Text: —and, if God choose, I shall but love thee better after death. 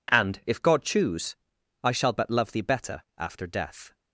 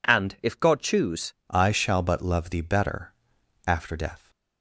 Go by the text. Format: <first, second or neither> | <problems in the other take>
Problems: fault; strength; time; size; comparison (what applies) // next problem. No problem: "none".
first | changes voice at "I"; from 1.4 s on; 2.8 s long // pauses between "better" and "after"; noticeable; at 3.1 s; 0.54 s long